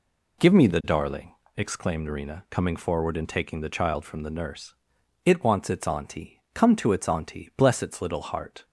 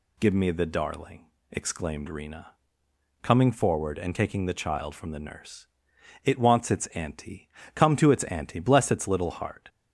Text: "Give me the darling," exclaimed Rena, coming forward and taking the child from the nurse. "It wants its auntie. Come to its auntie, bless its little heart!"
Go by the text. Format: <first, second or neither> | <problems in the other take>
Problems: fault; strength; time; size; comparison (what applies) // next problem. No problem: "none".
neither | none